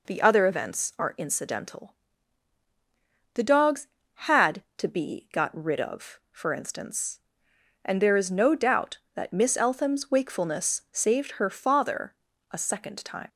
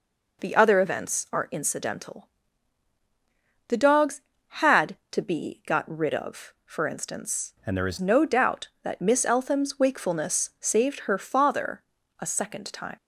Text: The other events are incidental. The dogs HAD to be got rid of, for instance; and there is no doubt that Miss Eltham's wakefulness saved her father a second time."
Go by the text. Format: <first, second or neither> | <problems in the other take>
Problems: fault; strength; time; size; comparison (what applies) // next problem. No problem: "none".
first | changes voice from "and" to "is"; from 7.6 to 7.9 s; 0.3 s long // pauses between "father" and "a"; slight; at 11.8 s; 0.36 s long; slight in the first